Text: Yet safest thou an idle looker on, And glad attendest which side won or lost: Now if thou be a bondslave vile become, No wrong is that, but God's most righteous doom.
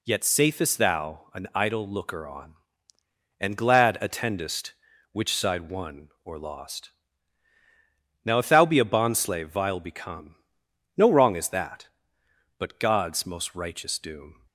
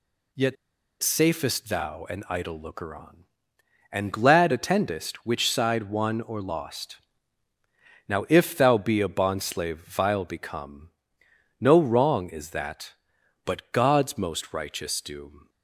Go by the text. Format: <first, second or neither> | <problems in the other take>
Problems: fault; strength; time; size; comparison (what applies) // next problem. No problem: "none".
first | pauses between "Yet" and "safest"; noticeable; at 0.5 s; 0.47 s long